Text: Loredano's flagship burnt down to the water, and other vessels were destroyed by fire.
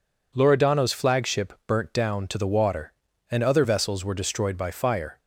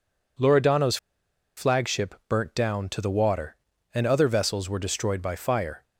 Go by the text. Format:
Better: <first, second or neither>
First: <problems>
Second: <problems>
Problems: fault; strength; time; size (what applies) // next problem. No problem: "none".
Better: first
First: none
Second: pauses between "Loredano's" and "flagship"; noticeable; at 0.9 s; 0.60 s long